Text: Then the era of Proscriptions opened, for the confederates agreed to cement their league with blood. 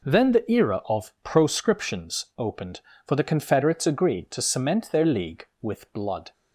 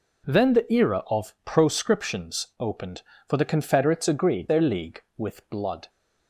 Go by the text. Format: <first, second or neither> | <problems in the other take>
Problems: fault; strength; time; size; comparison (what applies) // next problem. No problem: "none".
first | skips "to cement"; at 4.4 s